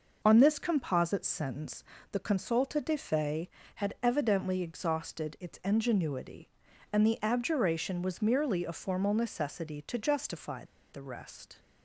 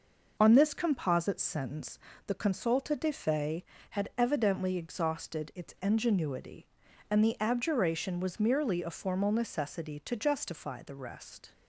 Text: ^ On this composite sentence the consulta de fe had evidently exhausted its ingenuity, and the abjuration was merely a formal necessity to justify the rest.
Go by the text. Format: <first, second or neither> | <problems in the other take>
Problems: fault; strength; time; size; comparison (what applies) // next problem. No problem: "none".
second | pauses between "sentence" and "the"; slight; at 1.8 s; 0.30 s long; slight in the second // pauses between "justify" and "the"; slight; at 10.6 s; 0.27 s long